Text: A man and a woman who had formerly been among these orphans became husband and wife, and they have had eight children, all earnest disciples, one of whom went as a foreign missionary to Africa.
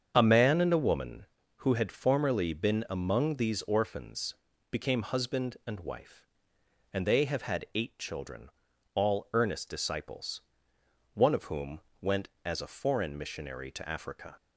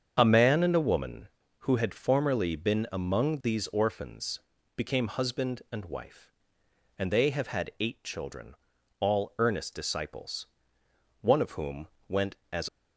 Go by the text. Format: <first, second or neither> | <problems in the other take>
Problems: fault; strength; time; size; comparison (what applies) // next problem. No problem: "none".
first | starts louder than the rest; strong; until 1.1 s; 7.5 dB; strong in the first // pauses between "orphans" and "became"; slight; at 4.3 s; 0.36 s long; slight in the first // pauses between "whom" and "went"; slight; at 11.8 s; 0.20 s long; slight in the first // stops before "a foreign missionary to Africa"; at 12.6 s